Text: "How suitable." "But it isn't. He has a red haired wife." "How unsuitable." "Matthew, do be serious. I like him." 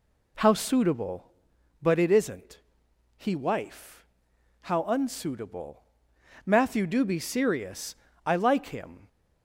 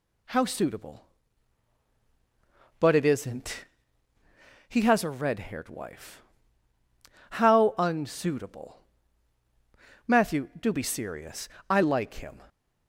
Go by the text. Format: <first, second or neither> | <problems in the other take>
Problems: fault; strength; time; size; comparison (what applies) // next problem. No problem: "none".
second | skips "has a red haired"; at 3.3 s